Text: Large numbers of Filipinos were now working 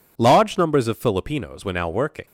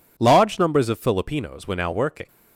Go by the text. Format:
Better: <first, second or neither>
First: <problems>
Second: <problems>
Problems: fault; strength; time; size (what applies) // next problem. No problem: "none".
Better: neither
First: none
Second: none